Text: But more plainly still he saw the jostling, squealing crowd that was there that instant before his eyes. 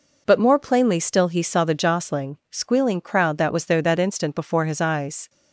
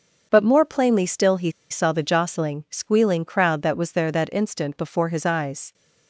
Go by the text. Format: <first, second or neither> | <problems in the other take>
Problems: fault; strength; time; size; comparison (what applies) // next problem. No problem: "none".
first | starts louder than the rest; until 1.3 s; 7 dB // pauses between "he" and "saw"; slight; at 1.5 s; 0.19 s long